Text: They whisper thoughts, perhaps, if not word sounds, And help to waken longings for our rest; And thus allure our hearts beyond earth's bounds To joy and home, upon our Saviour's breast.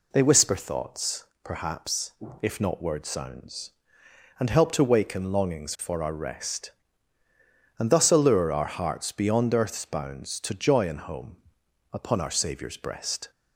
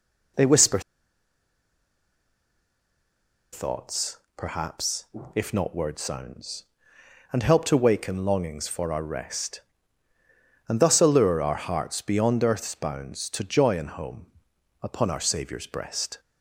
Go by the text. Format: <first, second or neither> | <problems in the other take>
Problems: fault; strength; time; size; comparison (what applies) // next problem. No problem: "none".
first | pauses between "whisper" and "thoughts"; strong; at 0.7 s; 2.7 s long